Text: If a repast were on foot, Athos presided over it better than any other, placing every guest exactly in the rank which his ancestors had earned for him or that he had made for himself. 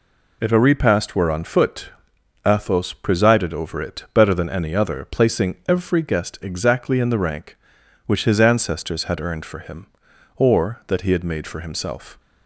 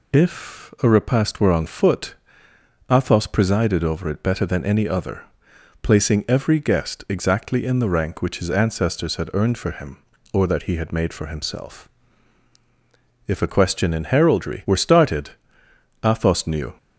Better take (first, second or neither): first